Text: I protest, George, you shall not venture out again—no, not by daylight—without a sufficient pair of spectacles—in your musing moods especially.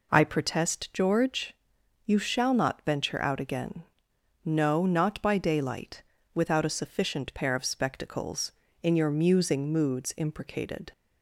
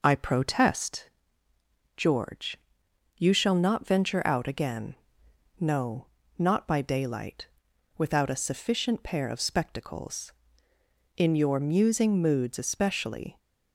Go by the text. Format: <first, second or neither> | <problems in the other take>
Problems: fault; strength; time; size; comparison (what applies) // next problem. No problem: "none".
second | says "imprecated" for "especially"; at 10.1 s